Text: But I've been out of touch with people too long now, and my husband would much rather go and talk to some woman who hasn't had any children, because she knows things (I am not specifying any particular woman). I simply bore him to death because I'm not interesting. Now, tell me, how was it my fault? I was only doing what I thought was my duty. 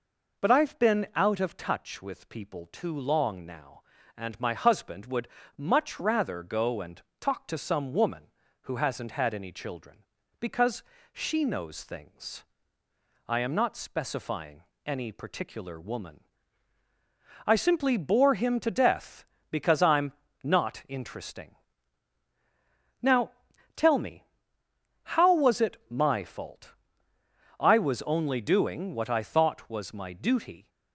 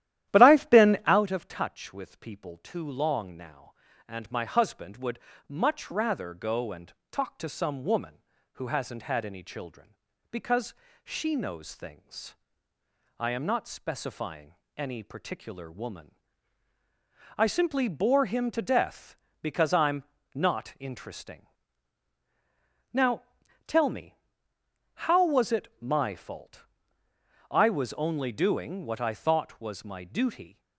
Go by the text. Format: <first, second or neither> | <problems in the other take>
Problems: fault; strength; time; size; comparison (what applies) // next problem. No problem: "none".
first | starts louder than the rest; strong; until 1.2 s; 12.5 dB // pauses between "would" and "much"; slight; at 5.1 s; 0.30 s long; slight in the first // pauses between "and" and "talk"; slight; at 6.9 s; 0.20 s long; slight in the first // pauses between "because" and "she"; slight; at 10.7 s; 0.30 s long; slight in the first // pauses between "specifying" and "any"; slight; at 14.5 s; 0.20 s long; slight in the first // pauses between "I'm" and "not"; slight; at 20.0 s; 0.30 s long; slight in the first